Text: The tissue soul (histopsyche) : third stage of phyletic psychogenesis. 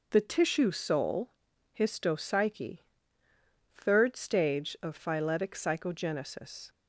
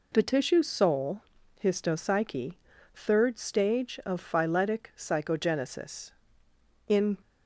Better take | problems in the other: first | goes on to say "In"; slight; from 6.8 s on; 0.28 s long

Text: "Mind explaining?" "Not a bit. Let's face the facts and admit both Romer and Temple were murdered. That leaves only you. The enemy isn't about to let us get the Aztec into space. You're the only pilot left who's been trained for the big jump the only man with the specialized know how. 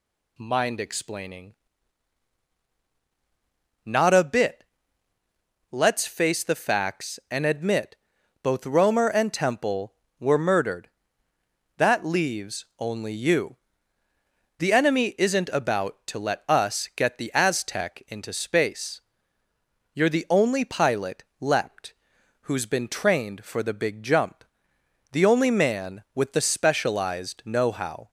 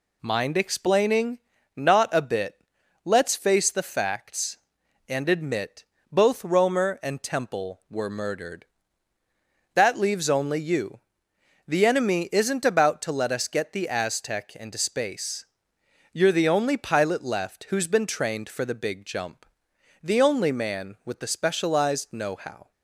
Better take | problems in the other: second | pauses between "admit" and "both"; noticeable; at 7.9 s; 0.48 s long; slight in the second // says "leapt" for "left"; at 21.3 s // pauses between "jump" and "the"; noticeable; at 24.4 s; 0.70 s long; noticeable in the second

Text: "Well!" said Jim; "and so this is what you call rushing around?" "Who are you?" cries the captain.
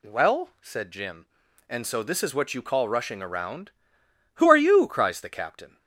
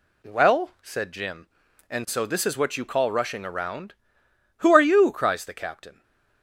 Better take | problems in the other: first | gets quieter; slight; throughout; 2 dB // stays silent after the last word; slight; from 5.9 s on; 0.5 s long

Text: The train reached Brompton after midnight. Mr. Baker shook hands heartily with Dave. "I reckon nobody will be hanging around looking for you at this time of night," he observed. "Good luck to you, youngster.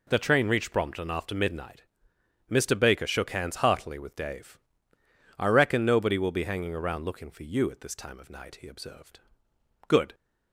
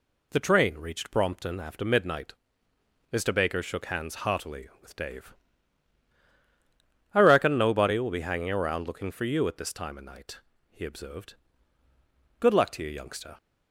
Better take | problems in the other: second | stops before "luck to you youngster"; at 10.1 s

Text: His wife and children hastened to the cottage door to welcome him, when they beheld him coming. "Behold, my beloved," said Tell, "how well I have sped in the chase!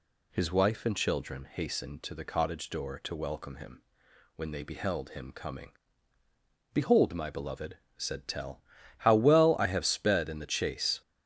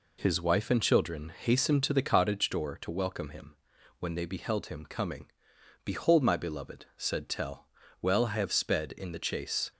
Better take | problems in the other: first | skips "how"; at 7.8 s

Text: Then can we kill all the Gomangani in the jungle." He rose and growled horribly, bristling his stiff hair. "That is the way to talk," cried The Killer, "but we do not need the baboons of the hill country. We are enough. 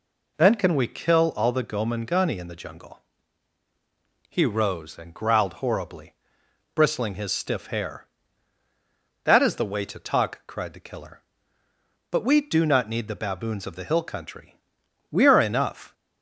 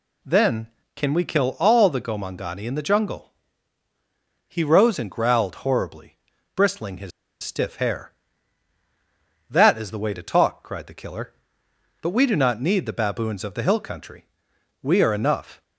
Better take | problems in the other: first | pauses between "his" and "stiff"; slight; at 7.1 s; 0.32 s long

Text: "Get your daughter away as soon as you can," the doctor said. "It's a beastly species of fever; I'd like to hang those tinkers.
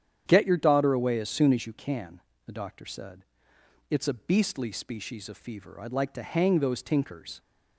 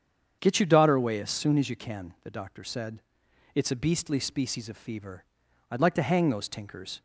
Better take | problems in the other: neither | starts louder than the rest; strong; the same in both

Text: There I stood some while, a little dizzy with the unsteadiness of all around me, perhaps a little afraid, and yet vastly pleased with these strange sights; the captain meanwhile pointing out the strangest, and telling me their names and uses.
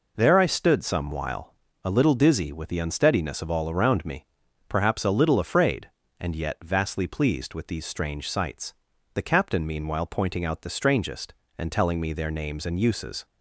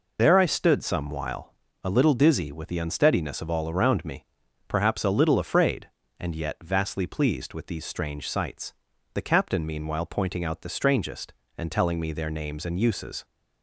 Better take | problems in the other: first | loses the start of "There"; at 0.1 s; 30 ms

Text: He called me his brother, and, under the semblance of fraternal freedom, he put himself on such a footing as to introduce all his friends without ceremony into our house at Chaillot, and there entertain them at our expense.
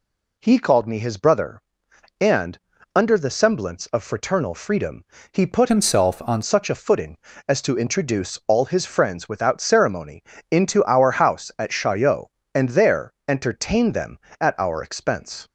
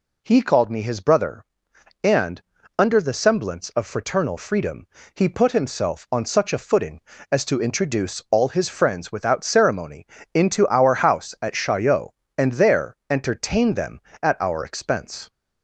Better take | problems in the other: second | changes voice from "himself" to "on"; from 5.6 to 6.4 s; 0.8 s long // pauses between "ceremony" and "into"; slight; at 10.2 s; 0.28 s long; slight in the second

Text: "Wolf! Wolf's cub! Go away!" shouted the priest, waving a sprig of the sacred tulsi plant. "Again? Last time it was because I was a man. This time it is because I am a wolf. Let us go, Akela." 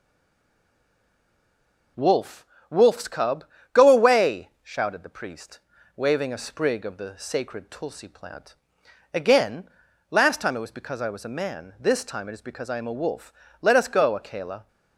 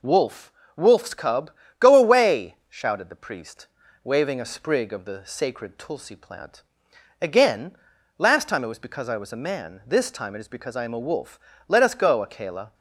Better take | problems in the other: second | stays silent before the first word; noticeable; until 1.9 s; 1.9 s long

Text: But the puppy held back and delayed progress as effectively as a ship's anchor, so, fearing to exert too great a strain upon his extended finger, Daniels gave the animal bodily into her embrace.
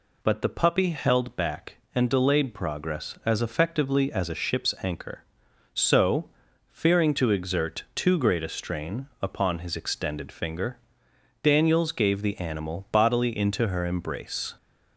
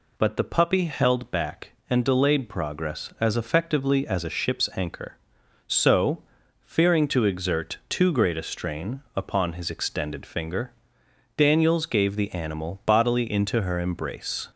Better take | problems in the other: neither | pauses between "strain" and "upon"; slight; the same in both

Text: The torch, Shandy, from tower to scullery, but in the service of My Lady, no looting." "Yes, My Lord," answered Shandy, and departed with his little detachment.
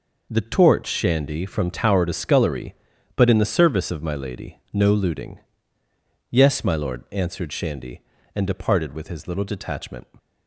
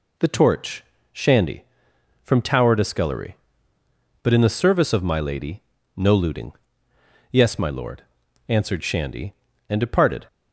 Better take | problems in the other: first | stops before "with his little detachment"; at 10.2 s

